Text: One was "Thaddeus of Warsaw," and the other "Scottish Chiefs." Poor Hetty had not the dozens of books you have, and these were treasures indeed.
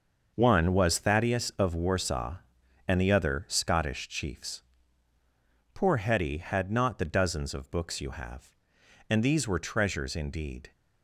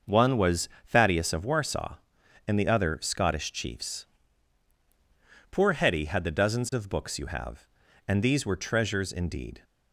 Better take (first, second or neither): first